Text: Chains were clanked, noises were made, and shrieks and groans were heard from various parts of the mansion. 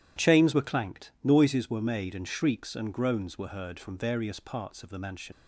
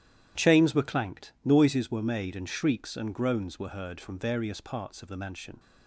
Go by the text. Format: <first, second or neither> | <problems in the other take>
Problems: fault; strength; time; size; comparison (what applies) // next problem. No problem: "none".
second | starts louder than the rest; strong; until 1.3 s; 11.5 dB; strong in the second // leaves "mansion" unfinished; at 5.3 s; 90 ms